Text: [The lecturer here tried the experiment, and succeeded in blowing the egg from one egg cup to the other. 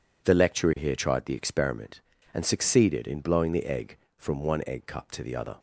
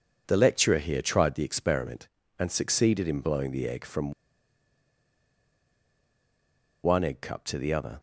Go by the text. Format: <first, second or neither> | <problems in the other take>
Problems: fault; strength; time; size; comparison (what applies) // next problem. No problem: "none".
first | pauses between "from" and "one"; strong; at 4.1 s; 2.7 s long